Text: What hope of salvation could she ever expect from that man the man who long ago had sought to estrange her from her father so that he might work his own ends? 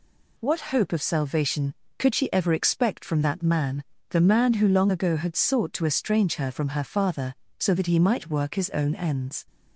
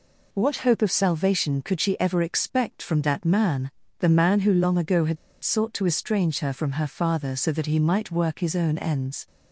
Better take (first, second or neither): first